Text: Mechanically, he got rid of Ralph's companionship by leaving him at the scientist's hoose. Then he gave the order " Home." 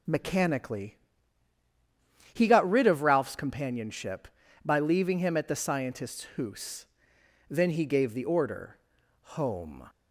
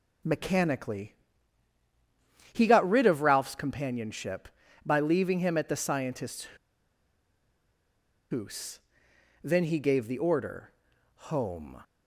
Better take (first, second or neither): first